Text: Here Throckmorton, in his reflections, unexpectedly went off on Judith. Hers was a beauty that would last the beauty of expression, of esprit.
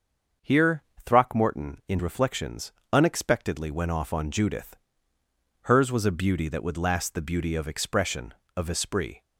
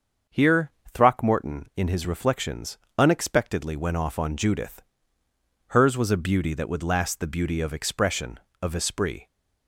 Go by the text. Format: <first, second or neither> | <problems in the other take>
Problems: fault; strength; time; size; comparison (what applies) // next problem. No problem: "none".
second | starts louder than the rest; until 1.6 s; 6.5 dB; also in the second // pauses between "Here" and "Throckmorton"; slight; at 0.8 s; 0.22 s long; slight in the second // skips "his"; at 2.0 s